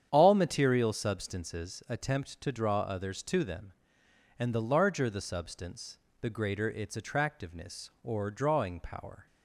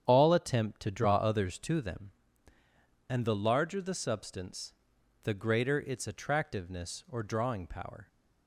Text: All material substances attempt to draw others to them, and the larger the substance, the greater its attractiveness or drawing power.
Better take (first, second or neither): first